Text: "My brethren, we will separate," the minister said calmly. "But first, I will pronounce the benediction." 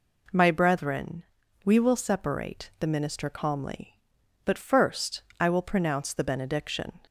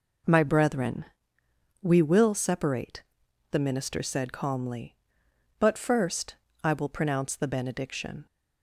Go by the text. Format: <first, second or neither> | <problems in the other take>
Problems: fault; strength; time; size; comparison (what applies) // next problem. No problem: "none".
second | skips "said"; at 3.2 s